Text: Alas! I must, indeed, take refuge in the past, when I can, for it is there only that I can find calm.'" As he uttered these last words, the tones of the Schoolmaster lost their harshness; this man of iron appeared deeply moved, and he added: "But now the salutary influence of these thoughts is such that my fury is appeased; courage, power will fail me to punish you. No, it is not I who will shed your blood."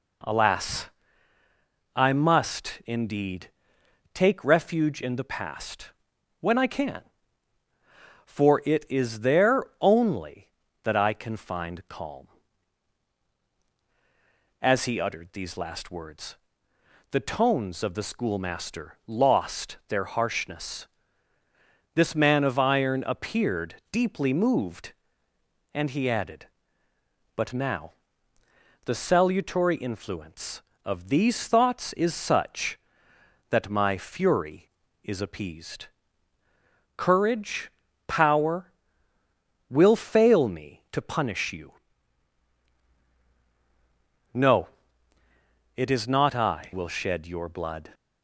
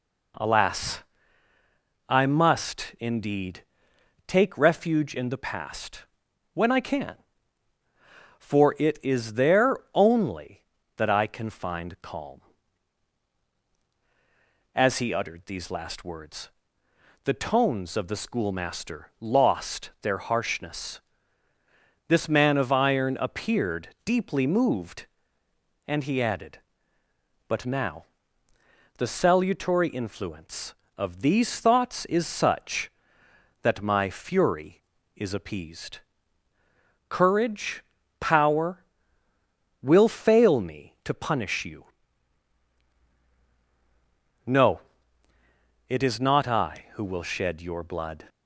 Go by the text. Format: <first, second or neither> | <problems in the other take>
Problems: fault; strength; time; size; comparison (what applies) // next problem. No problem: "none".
second | pauses between "there" and "only"; slight; at 9.6 s; 0.18 s long; slight in the second // pauses between "appeared" and "deeply"; slight; at 23.7 s; 0.16 s long; slight in the second // pauses between "now" and "the"; noticeable; at 27.9 s; 0.94 s long; noticeable in the second // skips "who"; at 46.7 s